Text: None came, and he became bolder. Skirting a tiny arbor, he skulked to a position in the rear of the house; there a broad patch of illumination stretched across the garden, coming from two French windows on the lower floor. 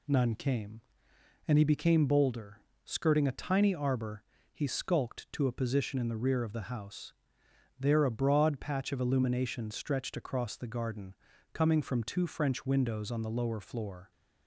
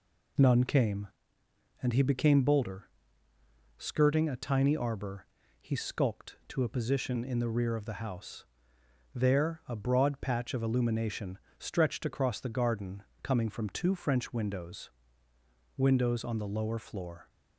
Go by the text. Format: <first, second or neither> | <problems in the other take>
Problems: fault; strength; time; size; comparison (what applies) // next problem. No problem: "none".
first | pauses between "illumination" and "stretched"; slight; at 11.3 s; 0.18 s long // says "windows" twice; at 15.7 s